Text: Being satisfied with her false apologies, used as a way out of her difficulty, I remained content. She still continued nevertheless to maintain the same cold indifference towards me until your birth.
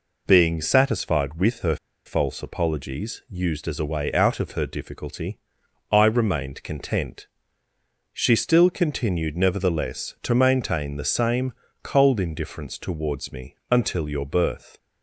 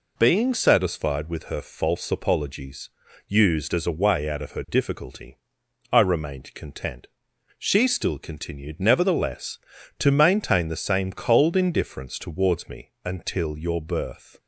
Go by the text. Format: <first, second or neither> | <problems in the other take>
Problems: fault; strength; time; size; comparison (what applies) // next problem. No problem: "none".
second | pauses between "her" and "false"; slight; at 1.7 s; 0.29 s long // pauses between "same" and "cold"; slight; at 11.5 s; 0.28 s long // pauses between "me" and "until"; slight; at 13.5 s; 0.16 s long; slight in the second